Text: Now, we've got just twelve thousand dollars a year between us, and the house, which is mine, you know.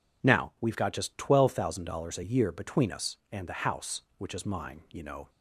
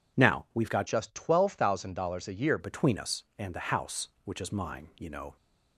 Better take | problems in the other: first | changes voice from "just" to "year"; from 0.8 to 2.5 s; 1.7 s long

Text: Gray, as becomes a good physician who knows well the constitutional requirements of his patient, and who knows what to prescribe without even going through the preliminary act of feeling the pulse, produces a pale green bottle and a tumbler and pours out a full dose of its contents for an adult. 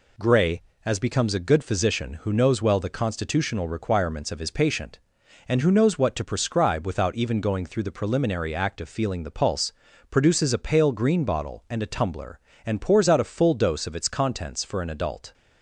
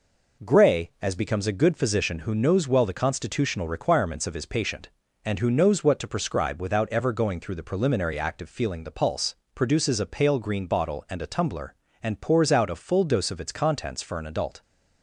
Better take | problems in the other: first | says "ever" for "even"; at 6.9 s

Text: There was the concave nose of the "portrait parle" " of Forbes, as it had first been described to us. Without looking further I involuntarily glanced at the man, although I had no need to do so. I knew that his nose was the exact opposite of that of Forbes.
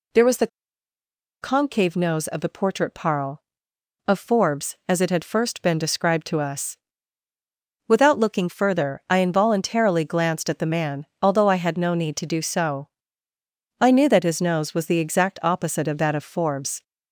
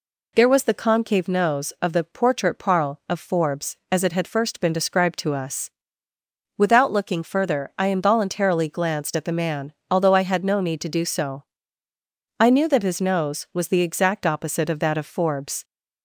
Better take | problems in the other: second | pauses between "the" and "concave"; noticeable; at 0.4 s; 0.94 s long

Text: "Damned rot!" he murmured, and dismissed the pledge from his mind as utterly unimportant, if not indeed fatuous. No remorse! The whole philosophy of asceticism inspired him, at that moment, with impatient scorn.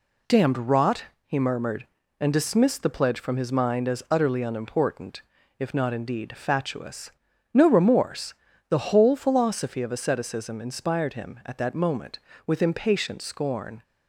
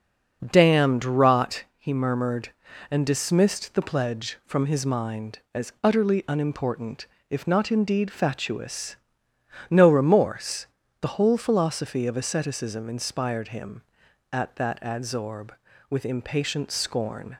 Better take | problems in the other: first | says "adsorb" for "moment"; at 14.8 s

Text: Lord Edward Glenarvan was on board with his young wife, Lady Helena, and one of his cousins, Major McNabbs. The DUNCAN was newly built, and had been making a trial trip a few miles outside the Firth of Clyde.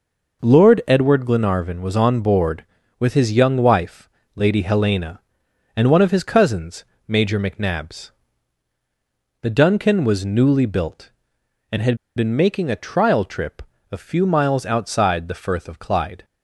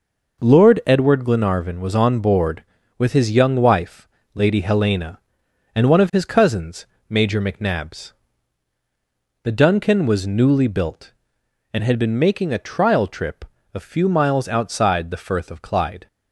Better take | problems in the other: second | pauses between "had" and "been"; slight; at 11.9 s; 0.19 s long // pauses between "trip" and "a"; slight; at 13.6 s; 0.30 s long; slight in the second

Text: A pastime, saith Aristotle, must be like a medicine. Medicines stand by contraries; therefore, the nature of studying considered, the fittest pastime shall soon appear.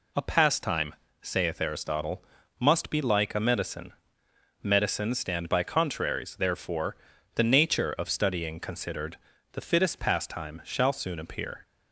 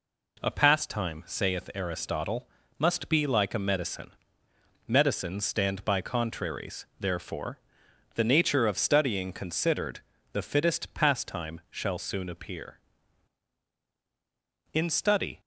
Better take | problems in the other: first | goes on to say "In study"; noticeable; from 14.7 s on; 0.68 s long

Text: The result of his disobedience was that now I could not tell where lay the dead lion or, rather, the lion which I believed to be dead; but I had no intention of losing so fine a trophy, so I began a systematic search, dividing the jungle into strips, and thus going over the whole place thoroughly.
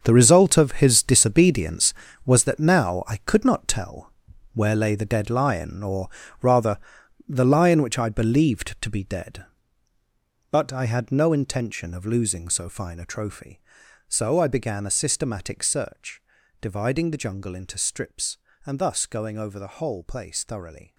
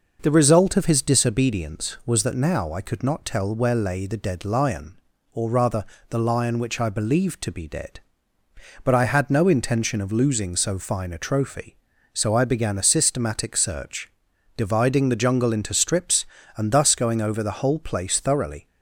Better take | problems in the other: second | gets quieter; strong; throughout; 13.5 dB // pauses between "tell" and "where"; at 4.1 s; 0.42 s long

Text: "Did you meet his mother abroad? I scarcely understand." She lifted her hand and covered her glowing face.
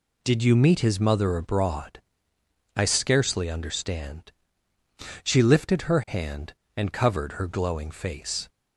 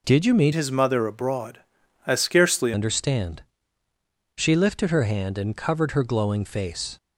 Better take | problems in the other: first | changes voice from "his" to "scarcely"; from 0.5 to 2.7 s; 2.2 s long

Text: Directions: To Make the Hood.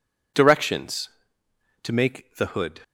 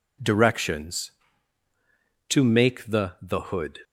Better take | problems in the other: first | says "the" twice; at 3.2 s

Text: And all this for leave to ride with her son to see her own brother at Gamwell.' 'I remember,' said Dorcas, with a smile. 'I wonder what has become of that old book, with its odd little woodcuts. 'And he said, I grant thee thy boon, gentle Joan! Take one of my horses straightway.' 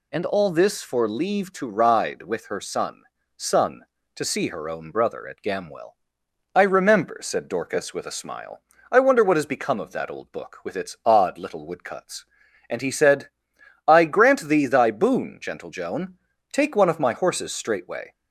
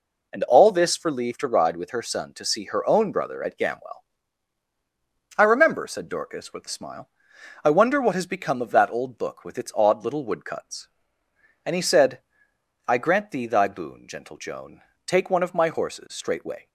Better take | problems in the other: second | says "son" twice; at 3.3 s

